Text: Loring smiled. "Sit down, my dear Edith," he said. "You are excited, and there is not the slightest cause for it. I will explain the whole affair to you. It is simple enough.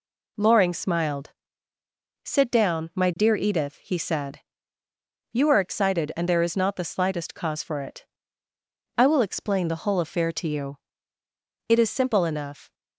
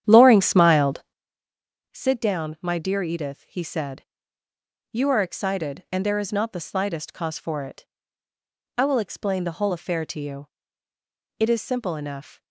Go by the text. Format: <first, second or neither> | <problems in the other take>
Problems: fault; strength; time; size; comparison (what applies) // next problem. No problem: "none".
first | starts louder than the rest; strong; until 1.6 s; 9.5 dB